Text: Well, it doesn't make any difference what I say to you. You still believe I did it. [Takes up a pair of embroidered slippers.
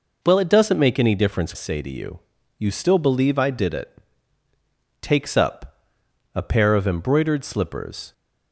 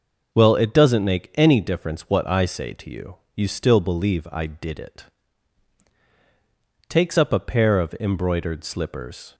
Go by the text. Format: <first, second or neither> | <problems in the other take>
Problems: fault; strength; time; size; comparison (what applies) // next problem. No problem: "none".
second | skips "what I"; at 1.5 s // pauses between "up" and "a"; noticeable; at 5.7 s; 0.58 s long